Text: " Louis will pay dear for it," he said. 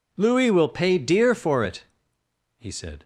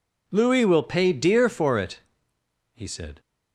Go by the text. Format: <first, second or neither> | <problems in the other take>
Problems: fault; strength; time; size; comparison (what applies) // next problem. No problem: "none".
neither | none